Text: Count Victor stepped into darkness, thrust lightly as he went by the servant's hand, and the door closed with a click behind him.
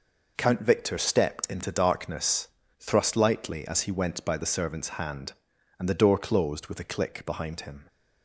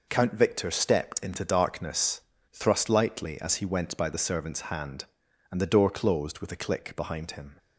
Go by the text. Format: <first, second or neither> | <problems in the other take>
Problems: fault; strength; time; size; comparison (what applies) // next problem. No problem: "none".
neither | none